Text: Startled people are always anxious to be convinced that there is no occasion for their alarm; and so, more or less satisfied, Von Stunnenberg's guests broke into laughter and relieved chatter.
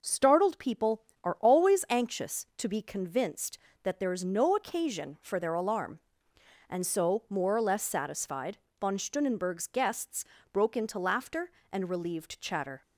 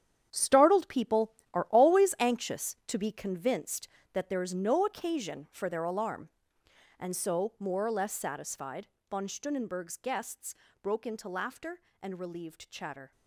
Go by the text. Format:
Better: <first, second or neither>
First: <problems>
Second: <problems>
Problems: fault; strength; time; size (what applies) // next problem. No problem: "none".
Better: first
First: pauses between "guests" and "broke"; slight; at 10.2 s; 0.28 s long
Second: gets quieter; strong; throughout; 11 dB // pauses between "guests" and "broke"; slight; at 10.5 s; 0.28 s long